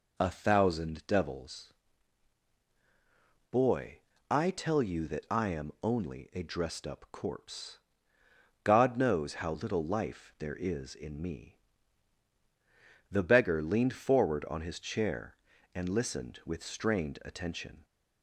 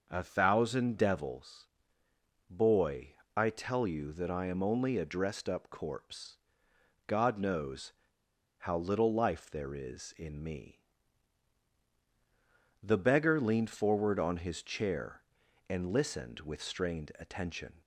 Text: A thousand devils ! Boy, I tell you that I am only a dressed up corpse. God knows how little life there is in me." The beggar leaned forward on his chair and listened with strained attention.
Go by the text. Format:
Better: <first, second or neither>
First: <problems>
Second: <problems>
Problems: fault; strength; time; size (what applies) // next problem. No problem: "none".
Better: first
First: none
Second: starts louder than the rest; noticeable; until 1.1 s; 6 dB // pauses between "knows" and "how"; noticeable; at 7.9 s; 0.66 s long